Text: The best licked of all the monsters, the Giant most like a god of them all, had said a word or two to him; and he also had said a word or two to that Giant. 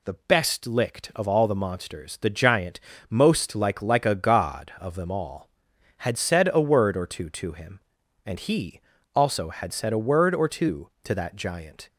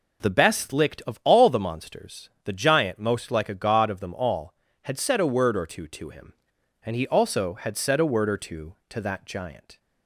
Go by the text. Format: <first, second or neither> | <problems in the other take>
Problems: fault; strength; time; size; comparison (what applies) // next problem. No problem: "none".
second | pauses between "Giant" and "most"; slight; at 2.8 s; 0.28 s long // says "like" twice; at 3.8 s // pauses between "he" and "also"; slight; at 8.8 s; 0.34 s long